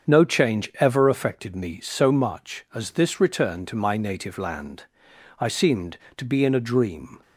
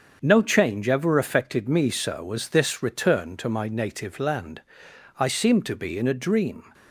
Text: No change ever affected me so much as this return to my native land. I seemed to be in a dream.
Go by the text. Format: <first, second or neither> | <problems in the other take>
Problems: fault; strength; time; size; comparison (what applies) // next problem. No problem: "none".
first | starts louder than the rest; strong; until 1.2 s; 7 dB; strong in the first // skips "much"; at 2.3 s